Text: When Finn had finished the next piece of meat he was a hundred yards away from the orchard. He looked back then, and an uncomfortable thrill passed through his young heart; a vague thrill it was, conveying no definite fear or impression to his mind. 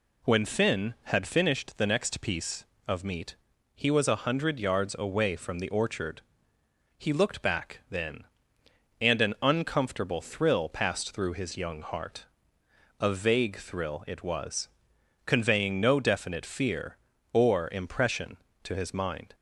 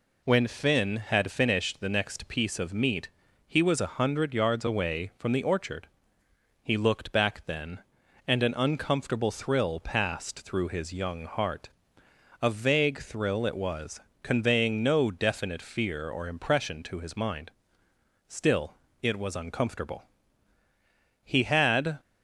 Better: first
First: pauses between "meat" and "he"; at 3.3 s; 0.40 s long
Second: pauses between "meat" and "he"; slight; at 3.0 s; 0.36 s long // goes on to say "Still it was uncomfortable He had"; strong; from 18.2 s on; 3.7 s long

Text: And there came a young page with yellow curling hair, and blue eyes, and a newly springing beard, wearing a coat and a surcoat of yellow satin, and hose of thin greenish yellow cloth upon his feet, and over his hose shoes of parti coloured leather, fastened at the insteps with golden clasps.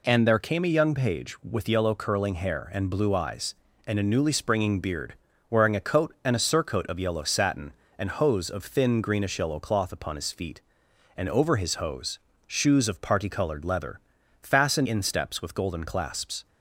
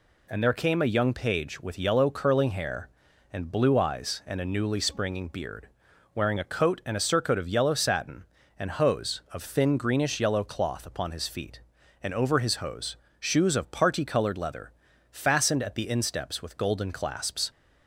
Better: second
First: pauses between "hose" and "shoes"; slight; at 12.1 s; 0.32 s long // skips "at the"; at 14.8 s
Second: pauses between "hose" and "shoes"; slight; at 12.9 s; 0.22 s long

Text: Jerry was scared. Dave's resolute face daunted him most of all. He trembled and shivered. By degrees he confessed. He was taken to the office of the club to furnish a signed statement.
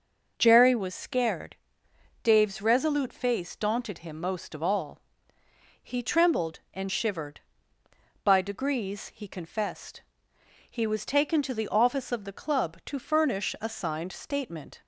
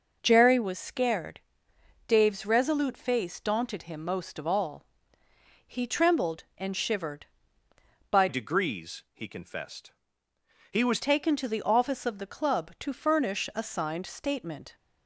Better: first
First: none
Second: changes voice from "degrees" to "was"; from 8.2 to 10.9 s; 2.7 s long

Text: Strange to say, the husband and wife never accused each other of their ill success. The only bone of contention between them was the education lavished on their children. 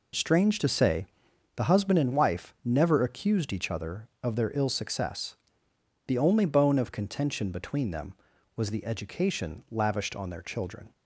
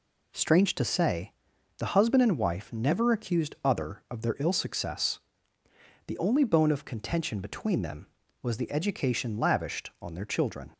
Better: first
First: none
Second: skips "each"; at 3.5 s

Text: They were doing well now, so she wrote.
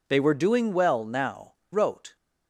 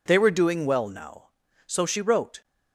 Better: second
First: skips "so she"; at 1.6 s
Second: none

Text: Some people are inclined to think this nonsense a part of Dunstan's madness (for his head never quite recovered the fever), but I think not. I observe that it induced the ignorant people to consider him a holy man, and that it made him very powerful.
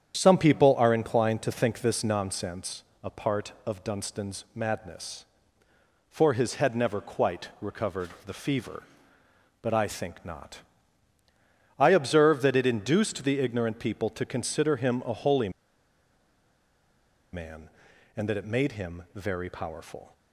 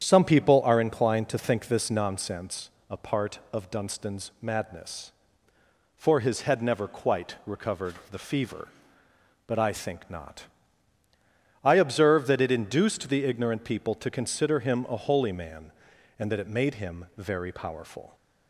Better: second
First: starts louder than the rest; strong; until 1.2 s; 9 dB // pauses between "nonsense" and "a"; slight; at 2.8 s; 0.20 s long // pauses between "recovered" and "the"; slight; at 8.0 s; 0.18 s long // pauses between "holy" and "man"; strong; at 15.4 s; 1.8 s long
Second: starts louder than the rest; strong; until 1.0 s; 9 dB // pauses between "nonsense" and "a"; slight; at 2.7 s; 0.20 s long // pauses between "recovered" and "the"; slight; at 7.9 s; 0.18 s long

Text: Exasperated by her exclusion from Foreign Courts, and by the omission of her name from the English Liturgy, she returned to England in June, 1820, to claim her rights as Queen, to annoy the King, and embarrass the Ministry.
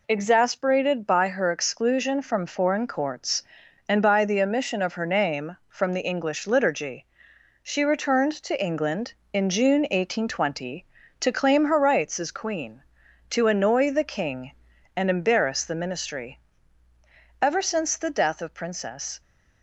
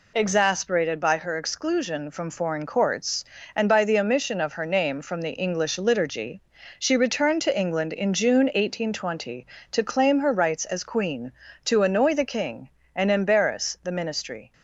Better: second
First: goes on to say "Ever since the death of Princess"; strong; from 17.4 s on; 1.8 s long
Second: none

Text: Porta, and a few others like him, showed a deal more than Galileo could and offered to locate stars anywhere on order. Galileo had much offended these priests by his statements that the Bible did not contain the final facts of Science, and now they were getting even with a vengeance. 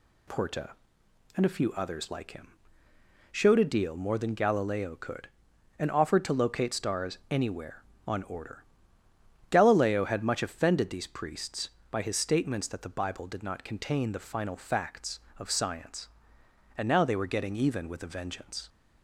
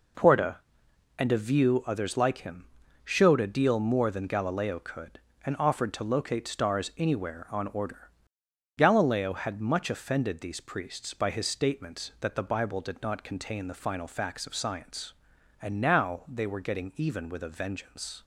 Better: first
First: none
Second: says "view" for "few"; at 1.3 s

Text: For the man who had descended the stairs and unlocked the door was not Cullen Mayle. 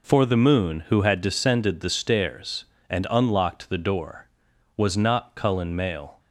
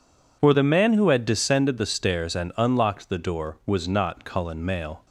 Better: second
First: says "moon" for "man"; at 0.3 s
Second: none

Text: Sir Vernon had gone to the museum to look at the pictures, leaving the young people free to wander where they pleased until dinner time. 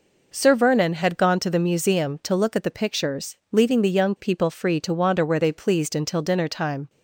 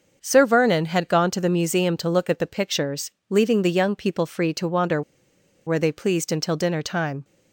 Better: first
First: none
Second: starts louder than the rest; until 1.2 s; 6.5 dB // pauses between "wander" and "where"; noticeable; at 5.0 s; 0.65 s long

